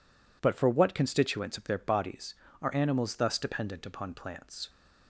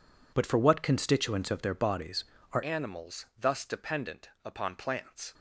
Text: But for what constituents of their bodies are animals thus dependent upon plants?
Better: first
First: none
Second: changes voice at "animals"; from 2.6 s on; 2.7 s long // pauses between "dependent" and "upon"; slight; at 4.2 s; 0.16 s long

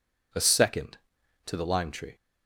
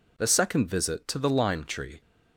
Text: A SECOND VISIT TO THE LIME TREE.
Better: second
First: skips "VISIT"; at 1.1 s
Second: none

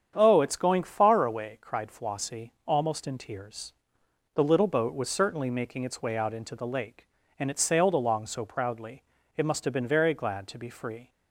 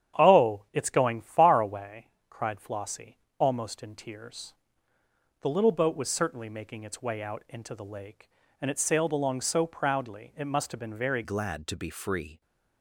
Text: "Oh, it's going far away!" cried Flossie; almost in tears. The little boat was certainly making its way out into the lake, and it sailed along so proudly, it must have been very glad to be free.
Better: first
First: starts louder than the rest; strong; until 1.1 s; 8 dB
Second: starts louder than the rest; strong; until 1.2 s; 9.5 dB // changes voice at "glad"; from 11.2 s on; 1.2 s long

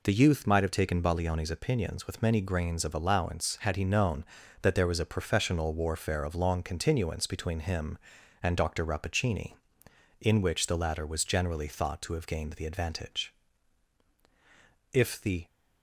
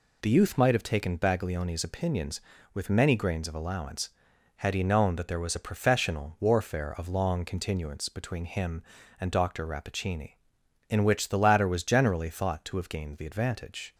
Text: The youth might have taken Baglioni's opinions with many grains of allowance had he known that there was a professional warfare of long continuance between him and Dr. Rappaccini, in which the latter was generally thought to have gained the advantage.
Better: second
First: goes on to say "If the"; from 14.9 s on; 0.54 s long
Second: none

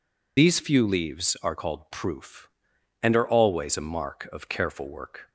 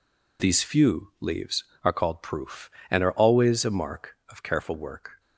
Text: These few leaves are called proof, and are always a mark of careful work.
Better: second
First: loses the start of "These"; at 0.3 s; 70 ms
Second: none

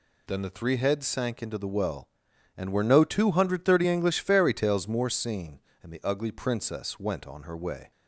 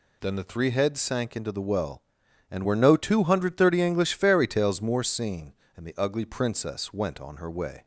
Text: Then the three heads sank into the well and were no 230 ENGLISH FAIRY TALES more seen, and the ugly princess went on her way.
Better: neither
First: none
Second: none

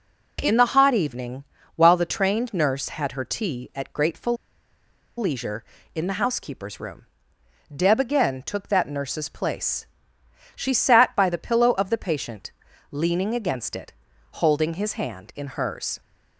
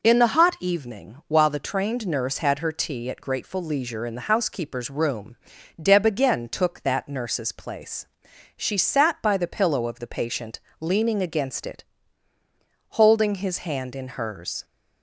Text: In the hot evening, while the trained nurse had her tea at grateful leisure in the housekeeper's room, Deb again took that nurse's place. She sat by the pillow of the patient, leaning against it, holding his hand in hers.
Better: second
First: pauses between "grateful" and "leisure"; noticeable; at 4.3 s; 0.82 s long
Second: none

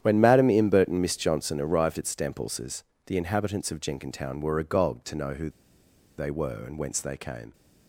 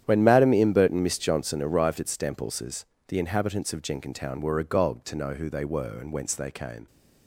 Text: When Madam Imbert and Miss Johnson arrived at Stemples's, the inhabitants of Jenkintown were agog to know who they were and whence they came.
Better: second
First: starts louder than the rest; strong; until 1.0 s; 10 dB // pauses between "who" and "they"; noticeable; at 5.5 s; 0.67 s long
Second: starts louder than the rest; strong; until 1.0 s; 10 dB

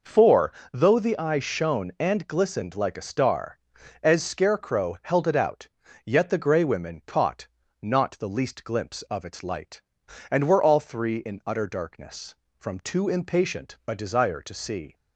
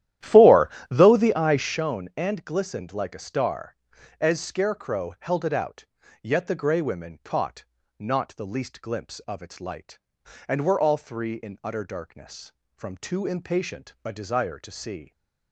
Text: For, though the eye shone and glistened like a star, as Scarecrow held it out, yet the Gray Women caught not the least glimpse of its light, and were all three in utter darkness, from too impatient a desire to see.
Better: first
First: pauses between "caught" and "not"; slight; at 7.4 s; 0.34 s long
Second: starts louder than the rest; strong; until 1.9 s; 12.5 dB // pauses between "caught" and "not"; slight; at 7.6 s; 0.34 s long

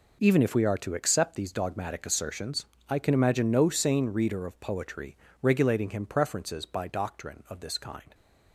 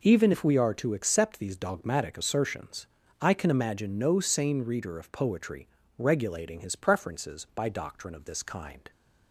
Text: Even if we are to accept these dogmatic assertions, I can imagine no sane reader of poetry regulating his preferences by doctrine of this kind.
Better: second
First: pauses between "poetry" and "regulating"; slight; at 5.1 s; 0.28 s long // says "him" for "his"; at 5.9 s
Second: pauses between "poetry" and "regulating"; slight; at 5.6 s; 0.30 s long

